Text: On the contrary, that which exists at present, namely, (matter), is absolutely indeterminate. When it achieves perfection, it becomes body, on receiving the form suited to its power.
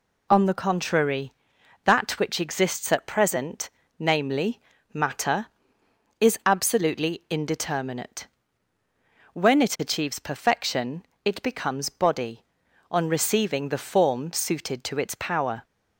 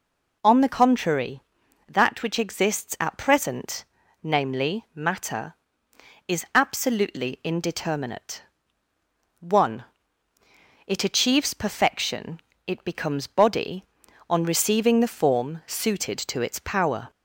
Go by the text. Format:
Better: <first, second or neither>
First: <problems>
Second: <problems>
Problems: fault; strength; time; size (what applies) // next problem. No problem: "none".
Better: first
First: none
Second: says "One" for "When"; at 9.3 s